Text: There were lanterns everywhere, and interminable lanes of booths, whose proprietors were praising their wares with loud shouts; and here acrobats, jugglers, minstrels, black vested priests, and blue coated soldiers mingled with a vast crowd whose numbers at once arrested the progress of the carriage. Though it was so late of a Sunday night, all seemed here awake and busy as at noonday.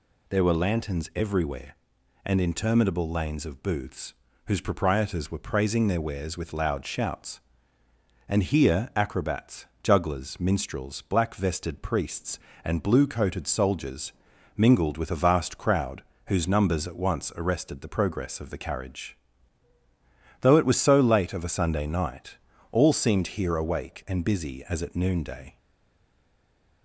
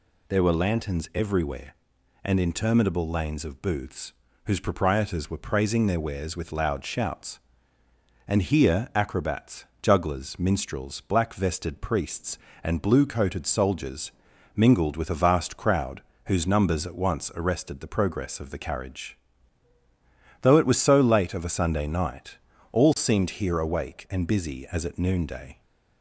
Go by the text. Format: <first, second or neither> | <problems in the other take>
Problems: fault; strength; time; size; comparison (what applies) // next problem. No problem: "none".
second | pauses between "soldiers" and "mingled"; noticeable; at 14.1 s; 0.46 s long; noticeable in the second // pauses between "crowd" and "whose"; slight; at 16.0 s; 0.24 s long; slight in the second // stays silent after the last word; noticeable; from 25.5 s on; 1.3 s long